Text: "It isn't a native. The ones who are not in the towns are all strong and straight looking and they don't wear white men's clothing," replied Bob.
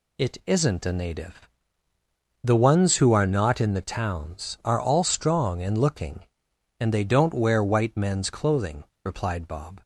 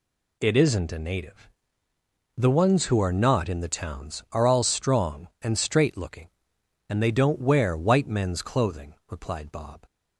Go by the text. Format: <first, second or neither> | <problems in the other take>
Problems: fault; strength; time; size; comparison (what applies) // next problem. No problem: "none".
second | skips "straight"; at 5.7 s